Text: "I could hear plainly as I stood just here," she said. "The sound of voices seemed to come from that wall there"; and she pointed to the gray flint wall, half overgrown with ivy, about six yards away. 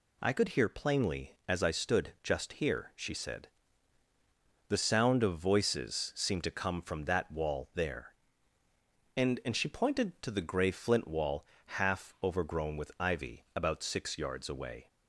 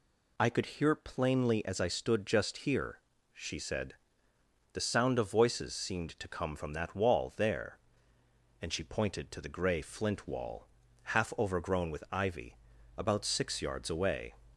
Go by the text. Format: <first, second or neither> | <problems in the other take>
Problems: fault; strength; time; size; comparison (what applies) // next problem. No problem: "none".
second | says "and" twice; at 9.4 s